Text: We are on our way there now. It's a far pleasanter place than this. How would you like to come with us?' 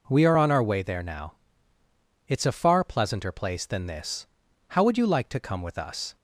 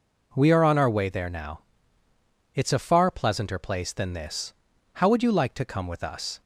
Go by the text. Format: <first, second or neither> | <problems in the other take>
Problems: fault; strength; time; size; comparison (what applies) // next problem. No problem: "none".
neither | none